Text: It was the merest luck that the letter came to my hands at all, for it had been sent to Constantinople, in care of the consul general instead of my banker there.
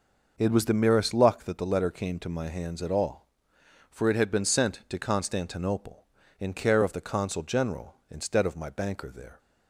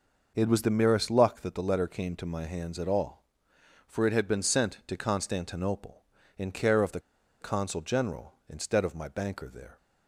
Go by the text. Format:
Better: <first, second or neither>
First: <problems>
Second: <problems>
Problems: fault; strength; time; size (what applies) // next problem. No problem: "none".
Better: first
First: none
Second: pauses between "the" and "consul"; at 6.9 s; 0.41 s long